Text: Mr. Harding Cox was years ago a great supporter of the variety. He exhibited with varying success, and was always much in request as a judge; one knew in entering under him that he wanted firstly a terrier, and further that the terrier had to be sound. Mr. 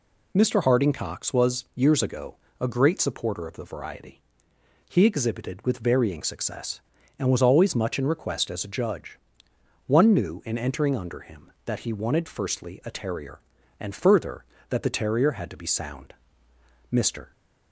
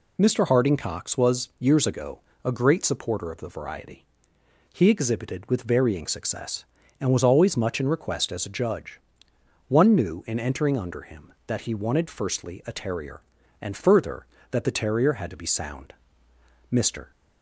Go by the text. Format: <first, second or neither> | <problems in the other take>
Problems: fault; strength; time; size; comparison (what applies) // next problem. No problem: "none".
neither | pauses between "ago" and "a"; slight; the same in both